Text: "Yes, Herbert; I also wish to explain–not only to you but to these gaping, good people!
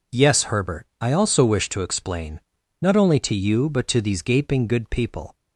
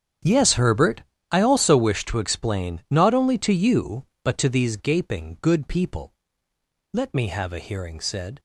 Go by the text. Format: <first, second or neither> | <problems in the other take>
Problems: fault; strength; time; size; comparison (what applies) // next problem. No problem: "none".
first | starts louder than the rest; strong; until 1.5 s; 8.5 dB // goes on to say "Let me have a hearing said"; from 6.9 s on; 1.4 s long